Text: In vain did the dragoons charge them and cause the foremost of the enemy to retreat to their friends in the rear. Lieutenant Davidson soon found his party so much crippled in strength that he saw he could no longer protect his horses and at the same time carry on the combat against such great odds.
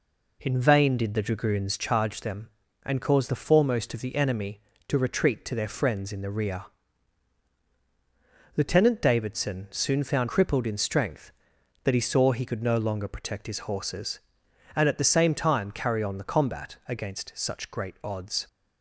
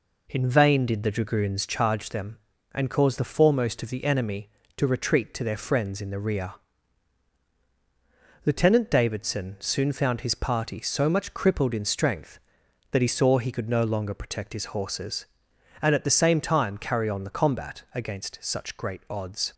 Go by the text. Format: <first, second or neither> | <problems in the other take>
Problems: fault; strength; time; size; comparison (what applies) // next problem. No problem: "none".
second | skips "his party so much"; at 10.2 s